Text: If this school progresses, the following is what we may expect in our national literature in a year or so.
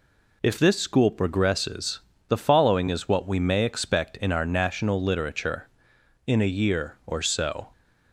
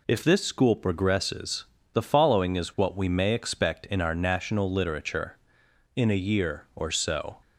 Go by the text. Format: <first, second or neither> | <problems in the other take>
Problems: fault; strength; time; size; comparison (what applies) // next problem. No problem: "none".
neither | none